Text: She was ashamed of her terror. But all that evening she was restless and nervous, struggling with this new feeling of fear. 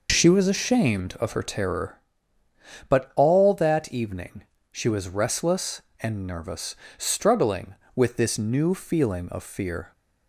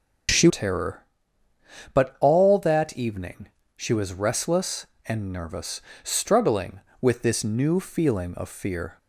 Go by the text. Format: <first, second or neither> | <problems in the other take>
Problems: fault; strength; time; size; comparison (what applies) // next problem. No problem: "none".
first | skips "was ashamed of her"; at 0.4 s // pauses between "evening" and "she"; slight; at 3.4 s; 0.30 s long; slight in the first